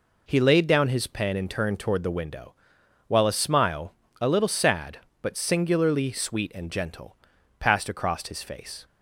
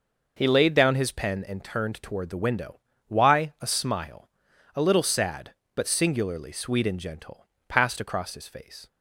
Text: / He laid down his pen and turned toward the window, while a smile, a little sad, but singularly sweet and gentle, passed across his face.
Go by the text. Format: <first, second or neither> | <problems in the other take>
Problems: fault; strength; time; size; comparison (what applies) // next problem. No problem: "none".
first | says "why" for "while"; at 3.0 s